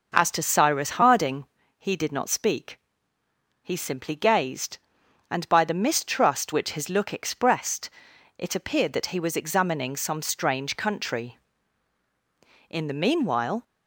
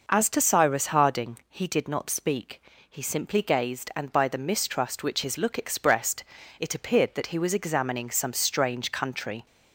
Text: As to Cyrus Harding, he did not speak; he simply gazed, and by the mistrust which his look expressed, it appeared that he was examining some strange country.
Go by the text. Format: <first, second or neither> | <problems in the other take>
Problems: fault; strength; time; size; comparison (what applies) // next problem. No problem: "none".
second | goes on to say "In the meanwhile"; noticeable; from 12.6 s on; 0.94 s long